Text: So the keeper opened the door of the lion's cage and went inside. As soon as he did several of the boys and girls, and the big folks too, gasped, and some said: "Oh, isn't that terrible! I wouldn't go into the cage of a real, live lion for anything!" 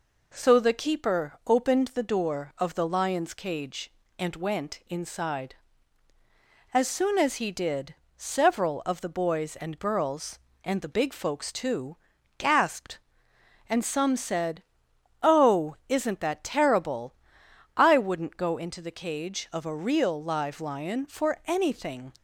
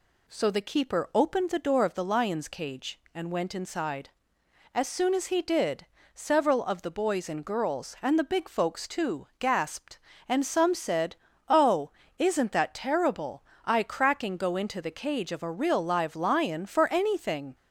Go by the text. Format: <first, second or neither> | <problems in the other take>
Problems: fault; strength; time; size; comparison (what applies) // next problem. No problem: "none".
first | pauses between "did" and "several"; slight; at 5.8 s; 0.30 s long; slight in the first // says "cracking" for "wouldn't"; at 13.8 s